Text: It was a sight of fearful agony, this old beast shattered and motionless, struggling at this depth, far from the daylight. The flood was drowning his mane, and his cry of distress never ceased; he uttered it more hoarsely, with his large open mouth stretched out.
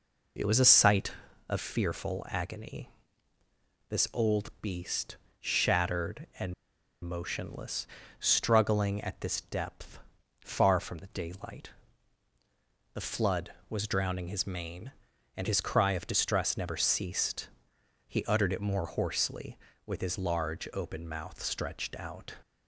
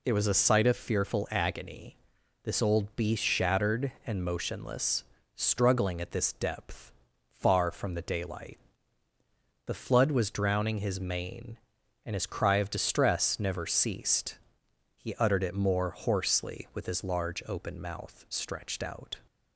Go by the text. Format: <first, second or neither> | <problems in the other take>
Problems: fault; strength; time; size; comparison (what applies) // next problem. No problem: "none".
second | pauses between "beast" and "shattered"; slight; at 5.1 s; 0.22 s long // pauses between "and" and "motionless"; noticeable; at 6.5 s; 0.49 s long